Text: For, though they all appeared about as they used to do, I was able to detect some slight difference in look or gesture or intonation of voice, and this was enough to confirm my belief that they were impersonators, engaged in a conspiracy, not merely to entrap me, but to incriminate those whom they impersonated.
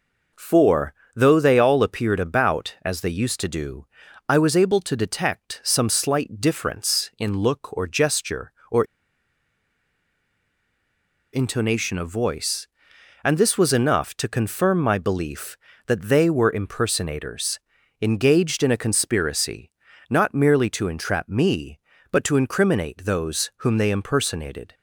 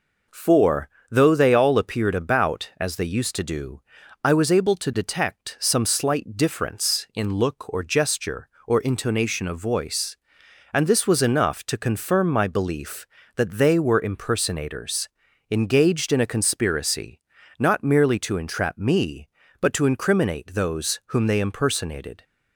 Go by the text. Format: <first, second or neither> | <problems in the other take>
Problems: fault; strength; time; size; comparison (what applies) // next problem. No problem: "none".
second | pauses between "or" and "intonation"; strong; at 8.8 s; 2.4 s long